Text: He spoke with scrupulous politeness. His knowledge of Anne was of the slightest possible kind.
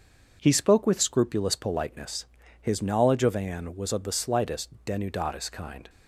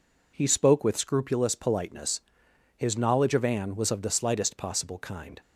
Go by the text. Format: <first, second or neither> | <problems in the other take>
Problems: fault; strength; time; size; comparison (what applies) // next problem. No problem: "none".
second | says "denudatis" for "possible"; at 4.8 s